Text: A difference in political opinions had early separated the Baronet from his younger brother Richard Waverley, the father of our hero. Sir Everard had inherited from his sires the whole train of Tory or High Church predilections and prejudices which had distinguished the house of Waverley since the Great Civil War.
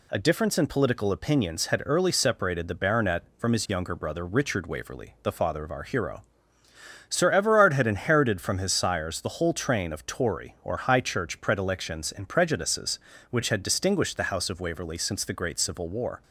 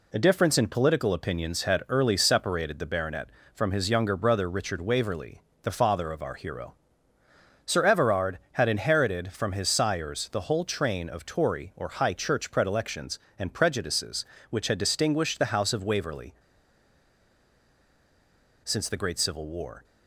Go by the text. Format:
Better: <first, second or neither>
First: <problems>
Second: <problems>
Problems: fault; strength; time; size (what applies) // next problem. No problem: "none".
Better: first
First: none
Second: pauses between "Waverley" and "since"; strong; at 16.3 s; 2.3 s long